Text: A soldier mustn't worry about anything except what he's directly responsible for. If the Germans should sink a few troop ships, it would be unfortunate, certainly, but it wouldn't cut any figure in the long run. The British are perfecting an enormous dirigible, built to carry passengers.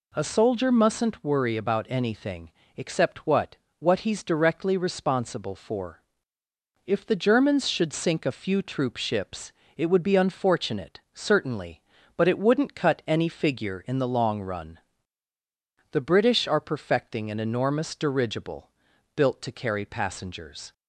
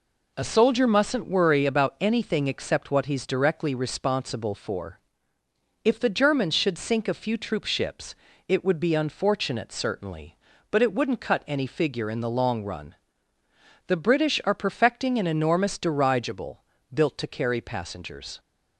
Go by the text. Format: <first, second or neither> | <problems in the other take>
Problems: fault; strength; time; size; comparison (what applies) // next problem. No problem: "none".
second | pauses between "anything" and "except"; slight; at 2.5 s; 0.26 s long // says "what" twice; at 3.7 s